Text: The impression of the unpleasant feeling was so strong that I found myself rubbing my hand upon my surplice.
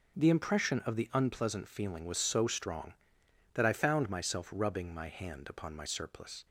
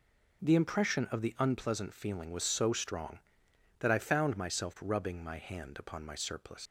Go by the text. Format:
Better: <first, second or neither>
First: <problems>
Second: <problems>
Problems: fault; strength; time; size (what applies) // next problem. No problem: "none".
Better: first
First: none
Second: leaves "surplice" unfinished; at 6.6 s; 110 ms